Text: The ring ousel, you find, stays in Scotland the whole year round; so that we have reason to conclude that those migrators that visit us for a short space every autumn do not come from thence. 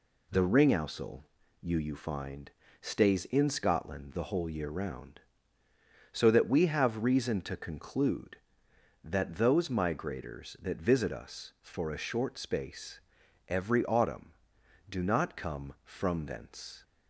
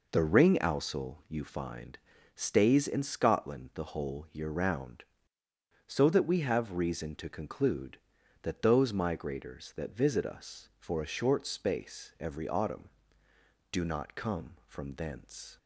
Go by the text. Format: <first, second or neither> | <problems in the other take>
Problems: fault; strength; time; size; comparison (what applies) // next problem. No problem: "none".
second | says "you" twice; at 1.7 s // pauses between "space" and "every"; noticeable; at 12.9 s; 0.48 s long